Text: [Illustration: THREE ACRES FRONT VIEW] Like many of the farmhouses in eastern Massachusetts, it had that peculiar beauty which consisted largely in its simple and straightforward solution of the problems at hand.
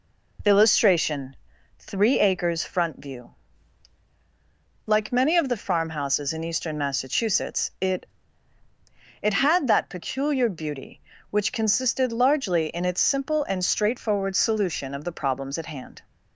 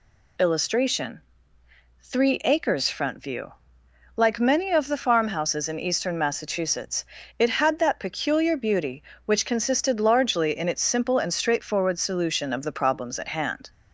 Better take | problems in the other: second | pauses between "VIEW" and "Like"; strong; at 3.3 s; 1.5 s long; noticeable in the second // says "it" twice; at 9.2 s

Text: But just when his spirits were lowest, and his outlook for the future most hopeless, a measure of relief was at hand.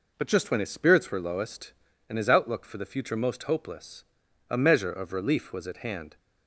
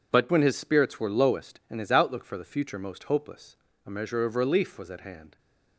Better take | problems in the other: first | skips "just"; at 0.3 s

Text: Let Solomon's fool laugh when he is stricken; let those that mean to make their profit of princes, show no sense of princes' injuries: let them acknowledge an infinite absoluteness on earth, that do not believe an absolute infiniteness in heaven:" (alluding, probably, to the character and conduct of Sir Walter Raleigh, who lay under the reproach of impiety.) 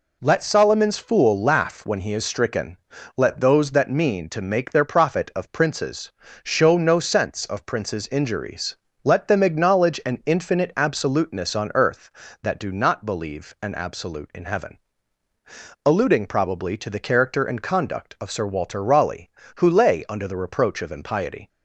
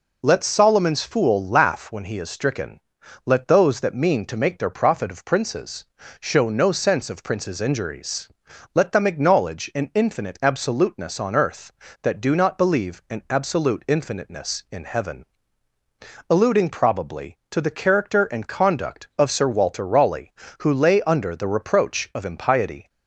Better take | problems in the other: second | skips "infiniteness"; at 14.3 s

